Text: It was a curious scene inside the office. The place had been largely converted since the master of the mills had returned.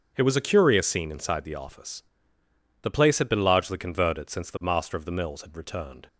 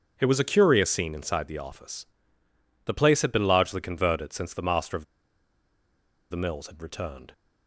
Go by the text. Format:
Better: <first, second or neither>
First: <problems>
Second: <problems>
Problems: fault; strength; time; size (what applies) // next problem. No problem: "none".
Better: first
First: starts louder than the rest; until 1.1 s; 6.5 dB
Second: starts louder than the rest; until 1.1 s; 6.5 dB // pauses between "of" and "the"; strong; at 5.0 s; 1.2 s long